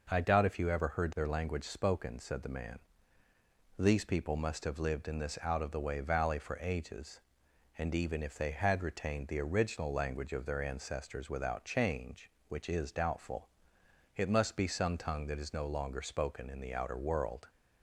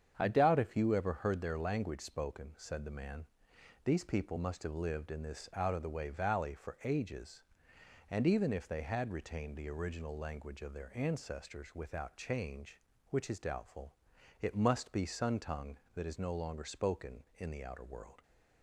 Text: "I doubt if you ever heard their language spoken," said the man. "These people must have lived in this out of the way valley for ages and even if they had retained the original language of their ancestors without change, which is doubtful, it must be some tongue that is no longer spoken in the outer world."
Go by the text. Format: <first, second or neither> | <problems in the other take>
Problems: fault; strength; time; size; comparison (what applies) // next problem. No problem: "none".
first | starts louder than the rest; strong; until 1.1 s; 8 dB // says "sun" for "some"; at 15.0 s